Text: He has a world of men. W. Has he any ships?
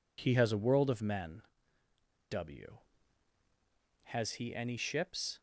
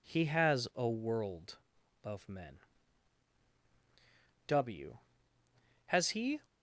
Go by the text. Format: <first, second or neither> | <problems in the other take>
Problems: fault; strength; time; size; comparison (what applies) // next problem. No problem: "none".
first | stops before "any ships"; at 6.4 s